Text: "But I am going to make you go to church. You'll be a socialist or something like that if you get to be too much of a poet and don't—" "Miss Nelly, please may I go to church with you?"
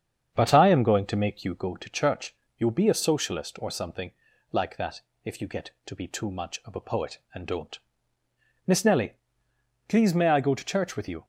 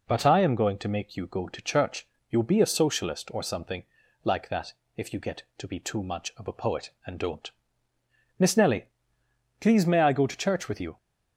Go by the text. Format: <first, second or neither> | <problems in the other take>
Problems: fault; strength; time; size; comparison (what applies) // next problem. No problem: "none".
second | starts louder than the rest; strong; until 1.7 s; 7.5 dB // pauses between "something" and "like"; at 4.1 s; 0.40 s long; also in the second // pauses between "that" and "if"; slight; at 5.0 s; 0.24 s long; slight in the second